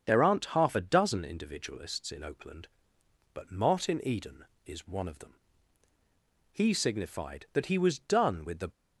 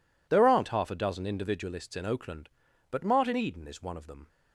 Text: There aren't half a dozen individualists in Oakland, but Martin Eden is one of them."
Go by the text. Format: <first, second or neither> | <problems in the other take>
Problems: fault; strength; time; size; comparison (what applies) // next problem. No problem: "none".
second | starts louder than the rest; strong; until 1.0 s; 7.5 dB // goes on to say "He signified that he was done with the"; strong; from 6.5 s on; 2.1 s long